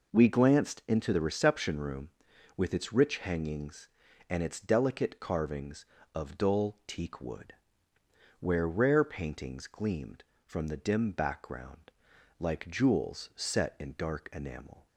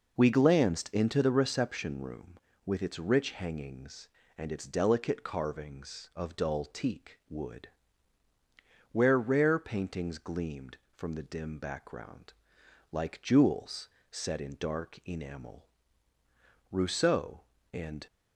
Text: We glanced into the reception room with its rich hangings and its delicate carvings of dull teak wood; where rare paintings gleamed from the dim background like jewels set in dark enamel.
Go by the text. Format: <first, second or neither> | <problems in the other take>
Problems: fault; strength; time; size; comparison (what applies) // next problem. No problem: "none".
first | pauses between "background" and "like"; noticeable; at 12.3 s; 0.60 s long; noticeable in the first // pauses between "jewels" and "set"; slight; at 13.8 s; 0.20 s long // goes on to say "Rousseau and"; from 16.7 s on; 1.3 s long